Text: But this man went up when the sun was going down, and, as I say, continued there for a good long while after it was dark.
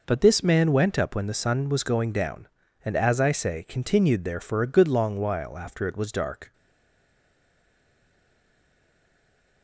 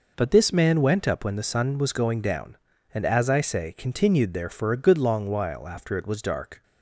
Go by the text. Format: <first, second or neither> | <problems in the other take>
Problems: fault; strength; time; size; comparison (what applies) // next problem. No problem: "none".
second | stays silent after the last word; strong; from 6.5 s on; 3.1 s long